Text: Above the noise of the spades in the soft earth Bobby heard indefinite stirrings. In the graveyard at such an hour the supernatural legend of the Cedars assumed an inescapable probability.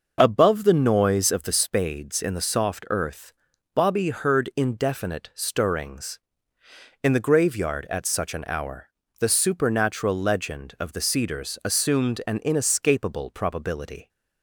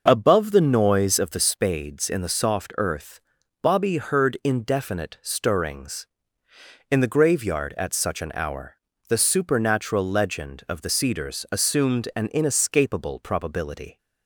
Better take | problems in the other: neither | starts louder than the rest; noticeable; the same in both // pauses between "earth" and "Bobby"; the same in both // pauses between "hour" and "the"; slight; the same in both

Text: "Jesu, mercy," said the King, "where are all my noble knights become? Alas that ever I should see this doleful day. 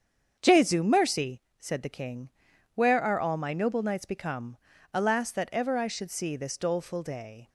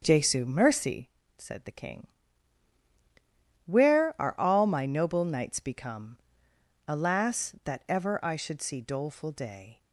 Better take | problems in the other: first | starts louder than the rest; until 1.0 s; 6.5 dB; strong in the first // skips "this"; at 8.8 s

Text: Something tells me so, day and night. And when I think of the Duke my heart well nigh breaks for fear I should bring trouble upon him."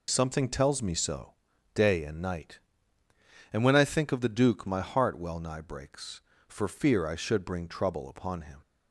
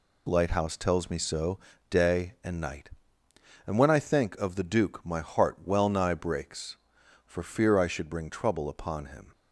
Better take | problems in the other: first | says "Lighthouse" for "Something"; at 0.2 s

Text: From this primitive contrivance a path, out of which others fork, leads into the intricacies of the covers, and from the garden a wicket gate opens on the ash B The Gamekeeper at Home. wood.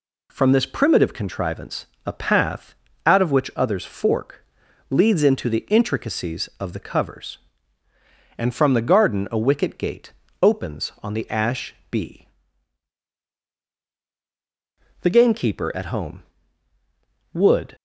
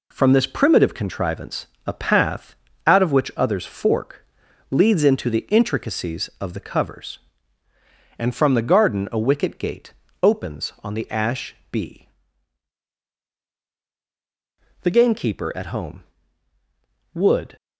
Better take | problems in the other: first | gets quieter; noticeable; throughout; 5 dB // pauses between "contrivance" and "a"; slight; at 1.6 s; 0.18 s long; slight in the first // pauses between "gate" and "opens"; slight; at 9.9 s; 0.28 s long; slight in the first // pauses between "ash" and "B"; slight; at 11.5 s; 0.16 s long; slight in the first // pauses between "B" and "The"; strong; at 12.0 s; 2.7 s long; strong in the first

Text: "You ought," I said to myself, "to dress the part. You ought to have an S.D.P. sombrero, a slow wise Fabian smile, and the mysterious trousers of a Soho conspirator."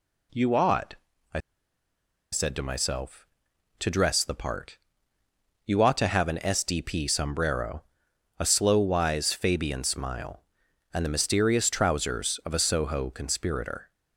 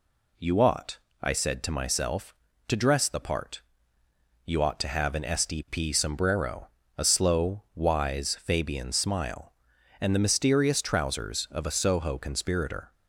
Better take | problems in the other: second | pauses between "I" and "said"; noticeable; at 1.3 s; 0.92 s long

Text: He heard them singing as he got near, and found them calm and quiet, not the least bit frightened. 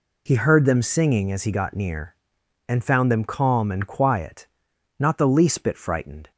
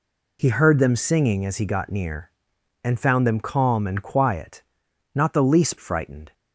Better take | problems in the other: first | skips "bit"; at 5.7 s

